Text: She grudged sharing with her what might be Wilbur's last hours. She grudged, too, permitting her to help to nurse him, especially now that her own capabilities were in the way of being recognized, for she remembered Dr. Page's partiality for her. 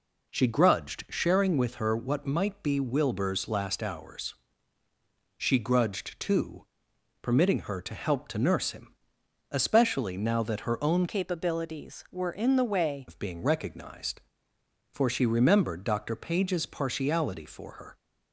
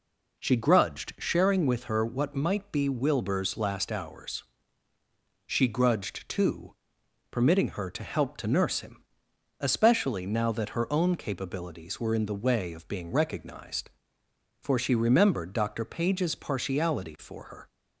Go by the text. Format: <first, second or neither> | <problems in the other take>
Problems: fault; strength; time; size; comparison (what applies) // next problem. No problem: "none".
second | changes voice from "capabilities" to "way"; from 11.0 to 13.0 s; 2.0 s long